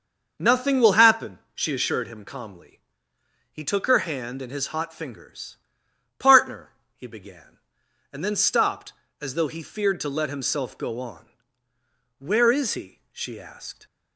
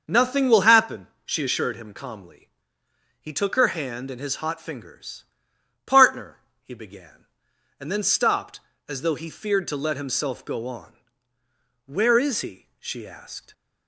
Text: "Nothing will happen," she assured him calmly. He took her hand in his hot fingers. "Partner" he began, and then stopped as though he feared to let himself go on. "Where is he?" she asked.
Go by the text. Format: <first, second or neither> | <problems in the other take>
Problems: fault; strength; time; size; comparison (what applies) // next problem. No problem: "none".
neither | starts louder than the rest; the same in both // pauses between "Partner" and "he"; slight; the same in both